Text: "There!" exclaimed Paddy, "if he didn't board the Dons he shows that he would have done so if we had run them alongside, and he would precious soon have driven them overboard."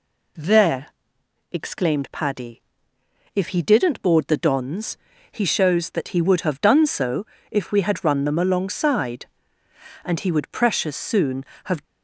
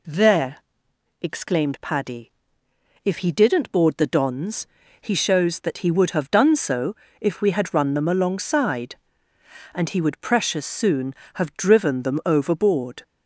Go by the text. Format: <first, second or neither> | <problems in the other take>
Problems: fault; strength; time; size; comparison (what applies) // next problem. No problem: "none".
second | pauses between "Dons" and "he"; slight; at 4.9 s; 0.34 s long; slight in the second // pauses between "so" and "if"; slight; at 7.2 s; 0.24 s long; slight in the second // stops before "driven them overboard"; at 11.8 s